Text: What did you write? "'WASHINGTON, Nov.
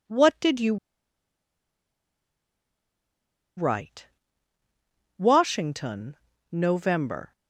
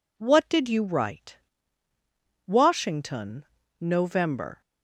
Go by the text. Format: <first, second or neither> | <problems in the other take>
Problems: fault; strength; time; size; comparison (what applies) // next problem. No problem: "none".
second | pauses between "you" and "write"; strong; at 0.7 s; 2.8 s long